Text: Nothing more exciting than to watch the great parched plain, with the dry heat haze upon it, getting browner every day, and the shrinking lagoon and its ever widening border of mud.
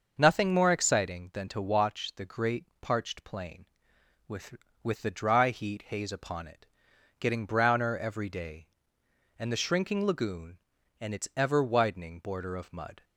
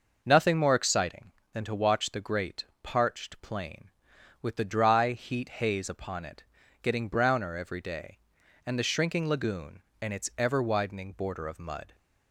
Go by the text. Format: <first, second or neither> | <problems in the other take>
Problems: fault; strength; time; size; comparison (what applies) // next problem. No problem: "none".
second | starts louder than the rest; until 1.1 s; 6.5 dB // pauses between "great" and "parched"; slight; at 2.6 s; 0.16 s long; slight in the second // says "with" twice; at 4.8 s